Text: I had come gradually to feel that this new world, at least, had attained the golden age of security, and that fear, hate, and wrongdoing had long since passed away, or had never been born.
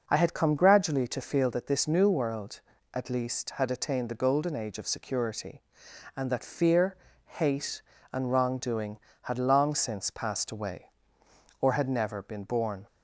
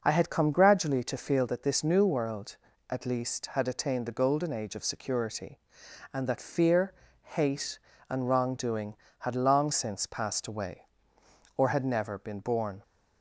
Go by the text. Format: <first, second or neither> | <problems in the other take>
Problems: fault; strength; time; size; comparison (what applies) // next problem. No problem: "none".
neither | none